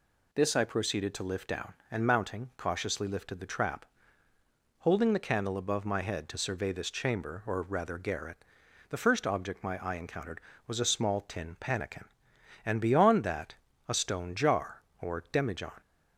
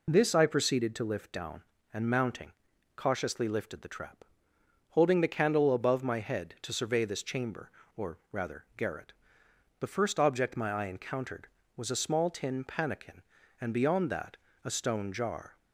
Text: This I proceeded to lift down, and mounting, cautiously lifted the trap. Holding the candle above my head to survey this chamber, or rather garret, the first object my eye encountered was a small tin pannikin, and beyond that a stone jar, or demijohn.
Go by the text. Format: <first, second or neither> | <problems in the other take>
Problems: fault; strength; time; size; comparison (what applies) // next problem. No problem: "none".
first | pauses between "or" and "rather"; slight; at 8.1 s; 0.16 s long // pauses between "that" and "a"; slight; at 14.3 s; 0.26 s long; slight in the first // stops before "or demijohn"; at 15.5 s